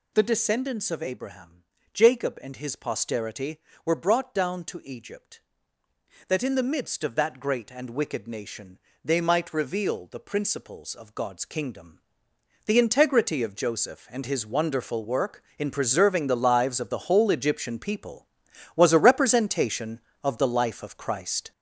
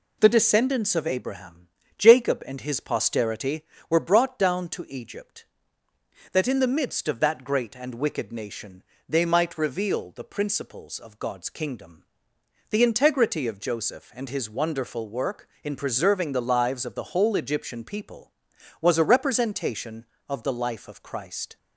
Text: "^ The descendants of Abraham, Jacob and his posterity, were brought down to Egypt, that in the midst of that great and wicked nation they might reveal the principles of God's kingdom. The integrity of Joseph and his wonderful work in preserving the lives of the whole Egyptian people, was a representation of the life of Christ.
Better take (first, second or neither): second